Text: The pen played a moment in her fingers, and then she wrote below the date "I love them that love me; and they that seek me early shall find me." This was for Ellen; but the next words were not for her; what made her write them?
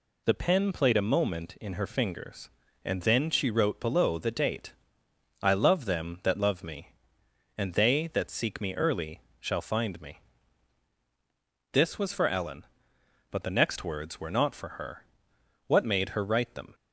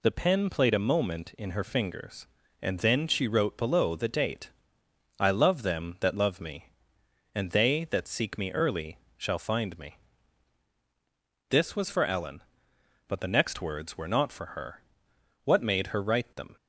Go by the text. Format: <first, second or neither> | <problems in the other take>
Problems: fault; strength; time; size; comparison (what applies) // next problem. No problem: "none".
neither | pauses between "date" and "I"; noticeable; the same in both // pauses between "early" and "shall"; slight; the same in both